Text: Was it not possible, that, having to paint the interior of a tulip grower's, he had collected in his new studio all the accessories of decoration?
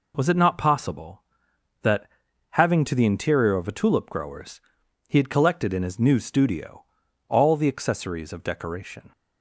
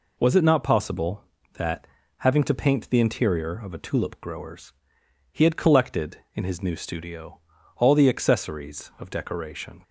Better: second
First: skips "paint"; at 2.9 s // pauses between "studio" and "all"; at 6.8 s; 0.44 s long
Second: pauses between "studio" and "all"; at 7.3 s; 0.38 s long

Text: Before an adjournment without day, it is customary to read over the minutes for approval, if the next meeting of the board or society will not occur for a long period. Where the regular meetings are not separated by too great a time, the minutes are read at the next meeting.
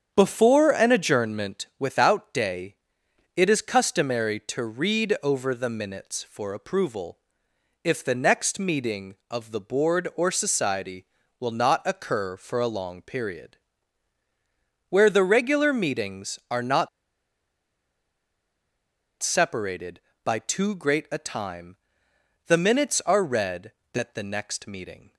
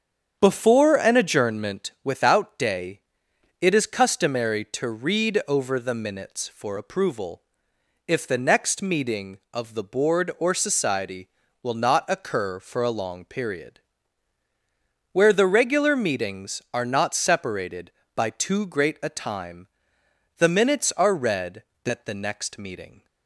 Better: second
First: starts louder than the rest; strong; until 1.1 s; 8 dB // pauses between "not" and "separated"; strong; at 16.8 s; 2.3 s long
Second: starts louder than the rest; strong; until 1.4 s; 8 dB

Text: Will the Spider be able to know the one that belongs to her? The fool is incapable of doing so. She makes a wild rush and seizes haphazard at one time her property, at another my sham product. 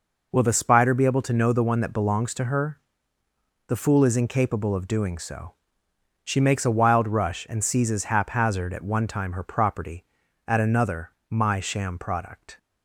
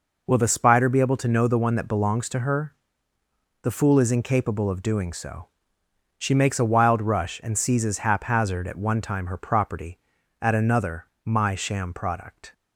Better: neither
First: pauses between "another" and "my"; slight; at 11.1 s; 0.18 s long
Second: pauses between "another" and "my"; slight; at 11.0 s; 0.18 s long

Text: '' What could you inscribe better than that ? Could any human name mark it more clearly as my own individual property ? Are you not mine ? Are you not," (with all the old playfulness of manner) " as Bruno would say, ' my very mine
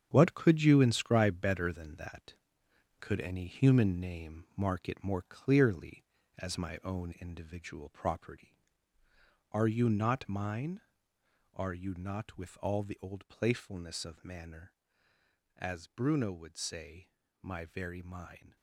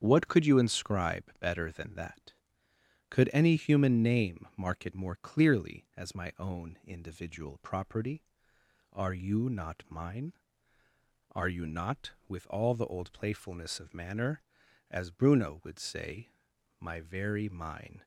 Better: second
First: gets quieter; strong; throughout; 14 dB // starts louder than the rest; strong; until 1.1 s; 8 dB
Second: starts louder than the rest; strong; until 1.0 s; 8 dB

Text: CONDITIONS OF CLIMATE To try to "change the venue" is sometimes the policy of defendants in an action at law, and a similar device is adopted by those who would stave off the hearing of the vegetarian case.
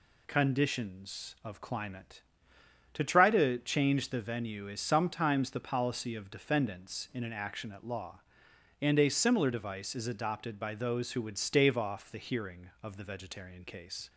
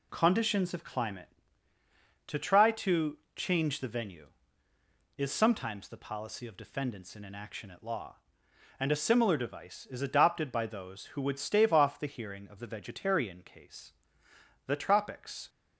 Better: first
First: none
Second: pauses between "to" and "change"; slight; at 3.1 s; 0.16 s long // goes on to say "The tropics"; noticeable; from 14.6 s on; 0.82 s long

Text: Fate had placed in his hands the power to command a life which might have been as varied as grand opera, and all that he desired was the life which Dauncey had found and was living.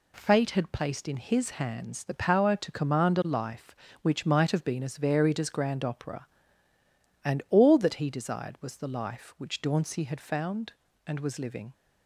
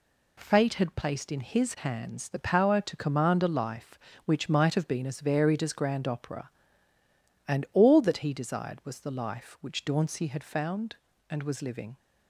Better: neither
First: none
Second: none

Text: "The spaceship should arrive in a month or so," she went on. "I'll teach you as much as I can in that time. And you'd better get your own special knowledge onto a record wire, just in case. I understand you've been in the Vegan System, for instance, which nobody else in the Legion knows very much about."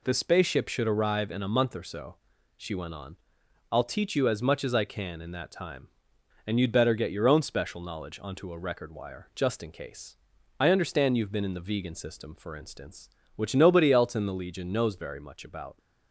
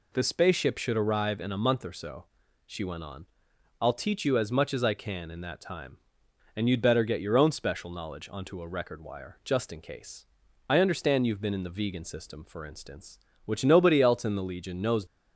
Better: first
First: none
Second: stops before "very much about"; at 15.0 s

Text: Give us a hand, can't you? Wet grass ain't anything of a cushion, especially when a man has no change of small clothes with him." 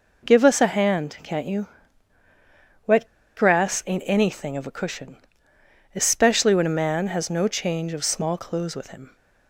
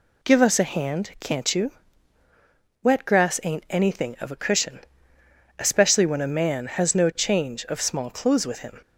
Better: second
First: pauses between "Wet" and "grass"; slight; at 3.0 s; 0.30 s long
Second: none

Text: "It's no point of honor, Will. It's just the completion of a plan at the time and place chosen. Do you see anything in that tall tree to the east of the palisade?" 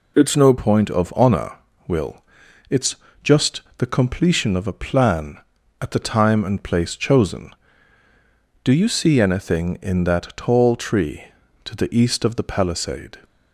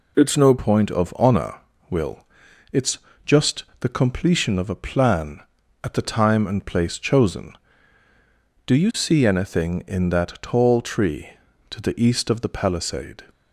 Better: neither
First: pauses between "It's" and "just"; slight; at 2.9 s; 0.26 s long // pauses between "just" and "the"; slight; at 3.6 s; 0.16 s long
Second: pauses between "It's" and "just"; slight; at 2.9 s; 0.26 s long // pauses between "just" and "the"; slight; at 3.6 s; 0.16 s long

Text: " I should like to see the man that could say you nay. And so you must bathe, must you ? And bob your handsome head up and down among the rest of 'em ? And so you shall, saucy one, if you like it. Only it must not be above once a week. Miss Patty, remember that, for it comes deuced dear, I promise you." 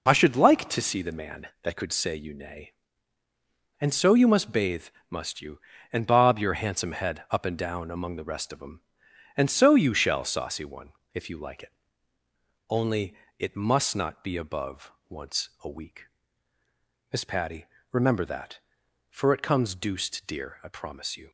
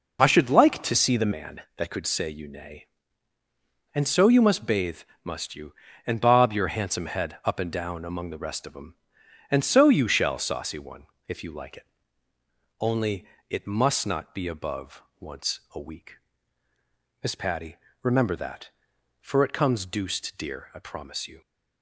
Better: first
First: pauses between "Only" and "it"; slight; at 13.1 s; 0.22 s long // pauses between "above" and "once"; slight; at 14.8 s; 0.18 s long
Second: changes voice from "see" to "the"; from 0.9 to 1.3 s; 0.4 s long // pauses between "Only" and "it"; slight; at 13.2 s; 0.22 s long // pauses between "above" and "once"; slight; at 15.0 s; 0.18 s long

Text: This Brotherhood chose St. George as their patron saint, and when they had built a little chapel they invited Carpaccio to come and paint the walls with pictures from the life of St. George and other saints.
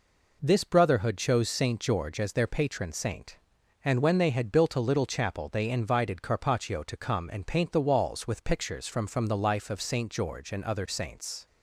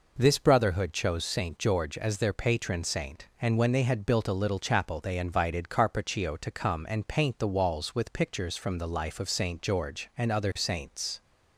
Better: second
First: says "from" twice; at 9.0 s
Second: none

